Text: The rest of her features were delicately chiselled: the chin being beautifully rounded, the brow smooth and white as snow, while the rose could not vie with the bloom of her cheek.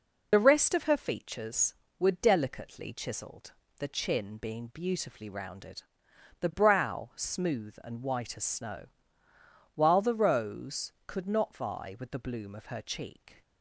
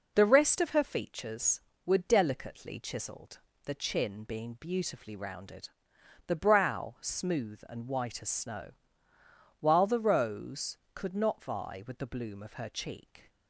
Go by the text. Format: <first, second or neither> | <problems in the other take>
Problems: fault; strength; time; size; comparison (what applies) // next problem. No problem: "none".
second | loses the start of "The"; at 0.3 s; 50 ms